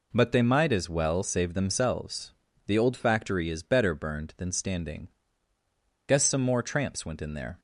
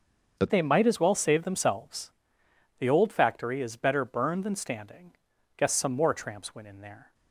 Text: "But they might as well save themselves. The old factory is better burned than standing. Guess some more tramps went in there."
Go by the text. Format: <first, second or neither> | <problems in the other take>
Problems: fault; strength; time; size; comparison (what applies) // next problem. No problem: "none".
first | starts louder than the rest; until 1.3 s; 6.5 dB // changes voice at "they"; from 0.4 s on; 6.7 s long